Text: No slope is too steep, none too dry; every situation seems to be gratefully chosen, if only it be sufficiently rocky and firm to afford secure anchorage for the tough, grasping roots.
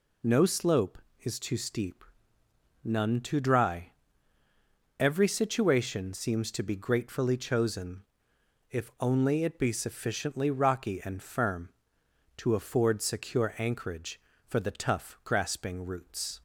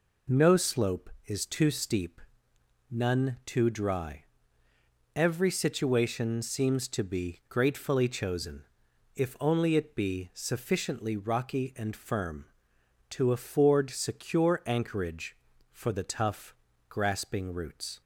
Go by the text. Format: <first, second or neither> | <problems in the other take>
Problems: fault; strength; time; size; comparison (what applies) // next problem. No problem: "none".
neither | none